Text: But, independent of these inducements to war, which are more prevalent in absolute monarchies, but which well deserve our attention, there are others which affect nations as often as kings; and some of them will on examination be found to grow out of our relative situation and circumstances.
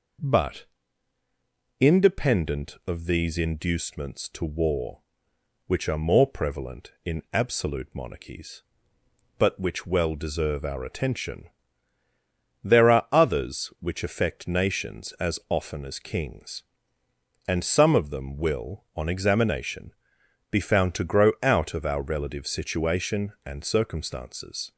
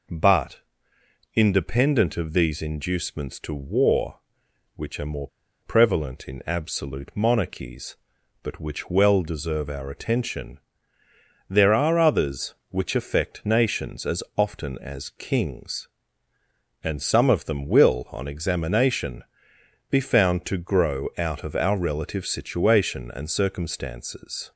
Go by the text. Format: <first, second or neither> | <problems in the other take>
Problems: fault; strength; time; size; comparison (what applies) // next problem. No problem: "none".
first | pauses between "more" and "prevalent"; slight; at 5.2 s; 0.35 s long // pauses between "examination" and "be"; noticeable; at 19.2 s; 0.66 s long; noticeable in the first